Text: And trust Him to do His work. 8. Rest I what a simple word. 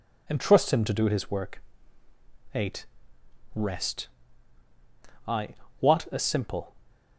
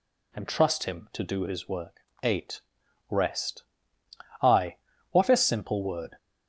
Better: second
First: pauses between "Rest" and "I"; at 4.0 s; 1.1 s long // pauses between "I" and "what"; slight; at 5.4 s; 0.30 s long // stops before "word"; at 6.8 s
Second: pauses between "Rest" and "I"; noticeable; at 3.6 s; 0.78 s long // pauses between "I" and "what"; slight; at 4.7 s; 0.34 s long

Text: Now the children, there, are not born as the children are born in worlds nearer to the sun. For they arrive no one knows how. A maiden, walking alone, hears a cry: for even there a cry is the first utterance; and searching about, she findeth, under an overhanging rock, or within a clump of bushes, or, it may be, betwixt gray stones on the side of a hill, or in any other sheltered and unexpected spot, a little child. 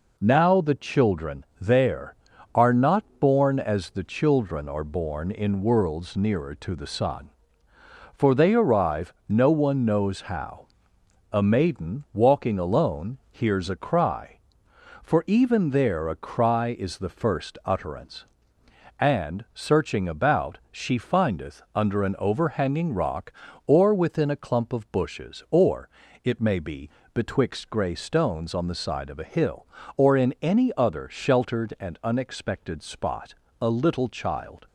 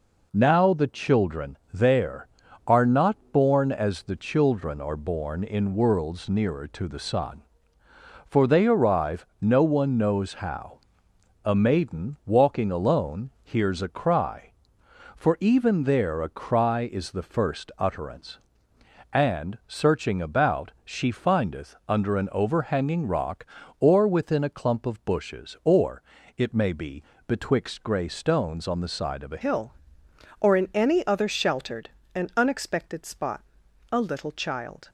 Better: first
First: pauses between "not" and "born"; slight; at 3.0 s; 0.16 s long // pauses between "arrive" and "no"; slight; at 9.1 s; 0.16 s long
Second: pauses between "not" and "born"; slight; at 3.1 s; 0.16 s long // pauses between "arrive" and "no"; slight; at 9.2 s; 0.16 s long // changes voice at "hill"; from 29.4 s on; 5.4 s long

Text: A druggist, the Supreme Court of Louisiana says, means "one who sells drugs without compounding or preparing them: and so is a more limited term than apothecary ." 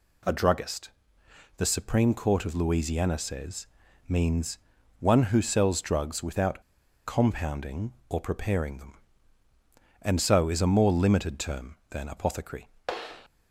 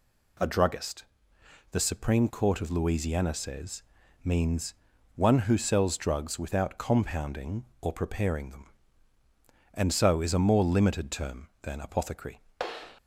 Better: second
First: pauses between "means" and "one"; at 4.5 s; 0.42 s long // pauses between "without" and "compounding"; at 6.6 s; 0.44 s long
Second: pauses between "means" and "one"; at 4.7 s; 0.42 s long

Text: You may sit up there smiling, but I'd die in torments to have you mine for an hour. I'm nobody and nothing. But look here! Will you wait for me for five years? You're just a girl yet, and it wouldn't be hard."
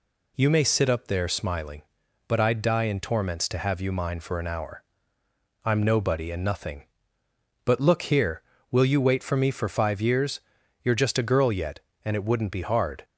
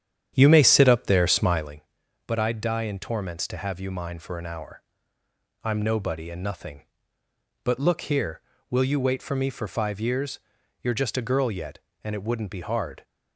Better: first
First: none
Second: starts louder than the rest; strong; until 1.8 s; 9.5 dB

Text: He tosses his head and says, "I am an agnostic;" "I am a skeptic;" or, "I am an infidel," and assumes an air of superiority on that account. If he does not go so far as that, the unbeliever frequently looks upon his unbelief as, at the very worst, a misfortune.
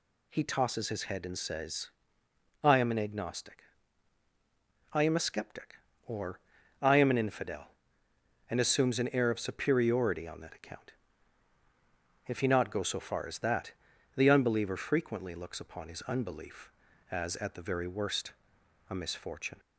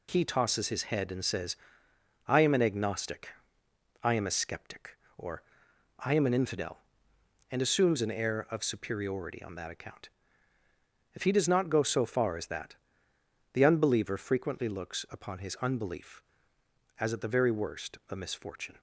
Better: second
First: skips "does"; at 12.4 s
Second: none

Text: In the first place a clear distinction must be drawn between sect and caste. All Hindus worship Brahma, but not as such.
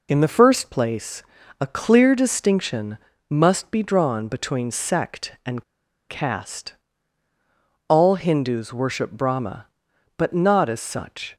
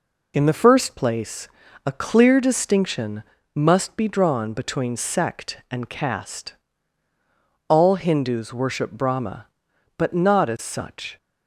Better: second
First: pauses between "place" and "a"; at 1.2 s; 0.38 s long // pauses between "distinction" and "must"; slight; at 2.9 s; 0.32 s long // pauses between "and" and "caste"; at 5.6 s; 0.45 s long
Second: pauses between "place" and "a"; at 1.4 s; 0.38 s long // pauses between "distinction" and "must"; slight; at 3.2 s; 0.32 s long

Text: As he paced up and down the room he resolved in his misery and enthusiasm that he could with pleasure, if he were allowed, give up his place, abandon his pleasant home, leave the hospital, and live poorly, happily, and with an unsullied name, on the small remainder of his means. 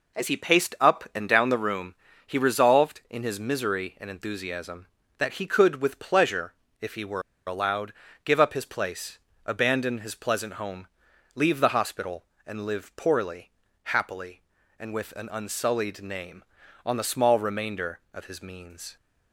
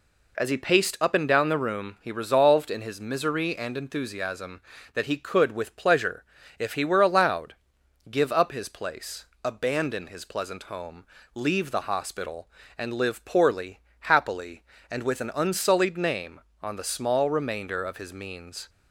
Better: second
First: pauses between "room" and "he"; slight; at 1.9 s; 0.32 s long // pauses between "were" and "allowed"; slight; at 7.2 s; 0.25 s long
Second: none

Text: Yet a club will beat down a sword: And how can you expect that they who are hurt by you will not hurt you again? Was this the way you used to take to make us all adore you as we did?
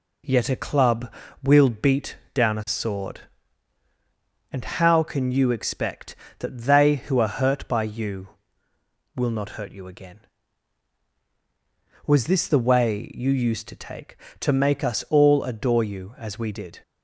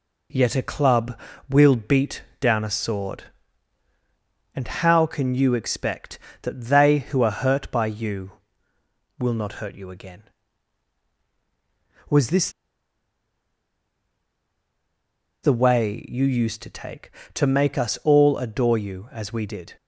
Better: first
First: pauses between "beat" and "down"; slight; at 2.1 s; 0.16 s long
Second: pauses between "beat" and "down"; slight; at 2.2 s; 0.16 s long // pauses between "this" and "the"; strong; at 12.4 s; 2.9 s long

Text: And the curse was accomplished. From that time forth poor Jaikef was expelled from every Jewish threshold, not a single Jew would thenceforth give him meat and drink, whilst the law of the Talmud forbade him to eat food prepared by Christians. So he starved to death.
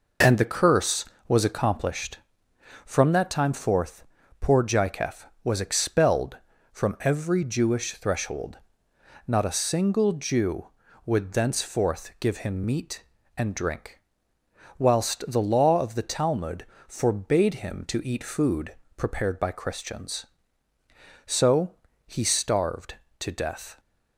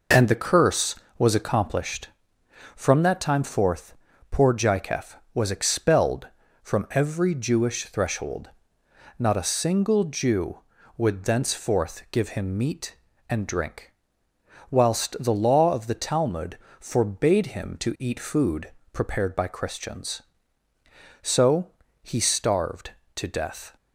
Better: neither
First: pauses between "forth" and "poor"; slight; at 4.0 s; 0.36 s long // pauses between "Talmud" and "forbade"; slight; at 16.6 s; 0.20 s long // pauses between "food" and "prepared"; slight; at 18.7 s; 0.22 s long // pauses between "So" and "he"; slight; at 21.7 s; 0.30 s long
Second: pauses between "forth" and "poor"; slight; at 3.9 s; 0.36 s long // pauses between "Talmud" and "forbade"; slight; at 16.5 s; 0.20 s long // pauses between "food" and "prepared"; slight; at 18.7 s; 0.22 s long // pauses between "So" and "he"; slight; at 21.7 s; 0.30 s long

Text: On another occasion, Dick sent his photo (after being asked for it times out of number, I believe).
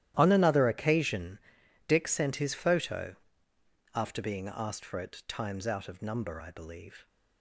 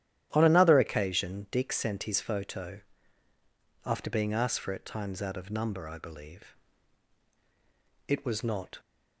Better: first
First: starts louder than the rest; strong; until 1.1 s; 13 dB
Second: starts louder than the rest; strong; until 1.3 s; 12.5 dB // goes on to say "It was not"; noticeable; from 8.0 s on; 0.70 s long

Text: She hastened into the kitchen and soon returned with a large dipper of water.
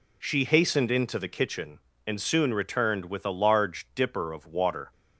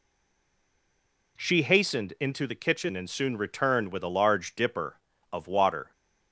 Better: first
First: none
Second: stays silent before the first word; noticeable; until 1.3 s; 1.3 s long

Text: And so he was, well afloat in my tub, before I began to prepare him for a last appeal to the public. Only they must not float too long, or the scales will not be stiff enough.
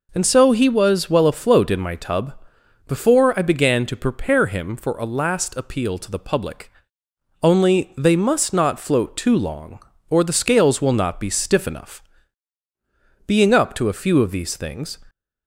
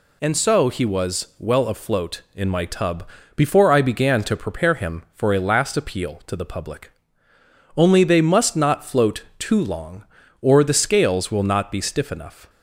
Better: second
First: goes on to say "Being up to a few of these things"; strong; from 13.2 s on; 1.7 s long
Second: none

